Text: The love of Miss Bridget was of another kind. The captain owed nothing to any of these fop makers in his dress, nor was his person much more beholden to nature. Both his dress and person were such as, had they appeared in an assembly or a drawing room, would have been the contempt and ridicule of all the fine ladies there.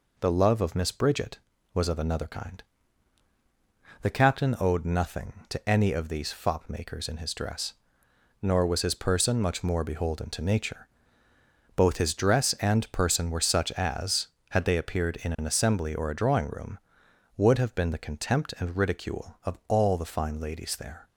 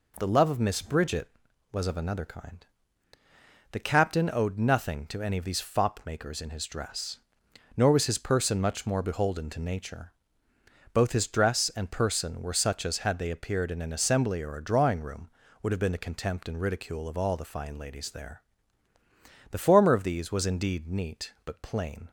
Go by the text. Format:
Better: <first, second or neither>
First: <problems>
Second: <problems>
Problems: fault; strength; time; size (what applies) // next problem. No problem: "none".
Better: first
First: none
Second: goes on to say "The former of these was indeed neat but plain"; strong; from 19.4 s on; 2.6 s long